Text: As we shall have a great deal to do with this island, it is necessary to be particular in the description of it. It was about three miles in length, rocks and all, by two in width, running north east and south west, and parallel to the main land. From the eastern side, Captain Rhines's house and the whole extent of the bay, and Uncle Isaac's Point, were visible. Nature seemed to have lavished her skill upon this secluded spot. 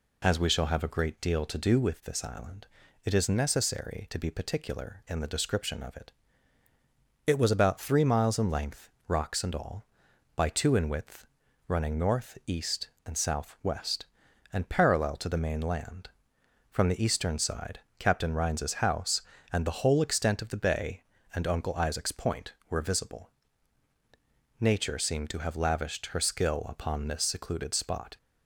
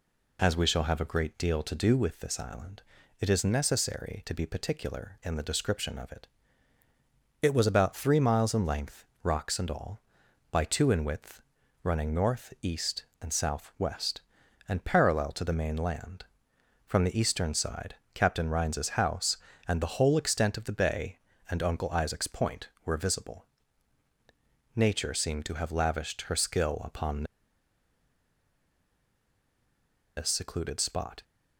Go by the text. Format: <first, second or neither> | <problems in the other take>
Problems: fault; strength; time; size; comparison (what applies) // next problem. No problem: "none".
first | pauses between "upon" and "this"; strong; at 27.2 s; 2.9 s long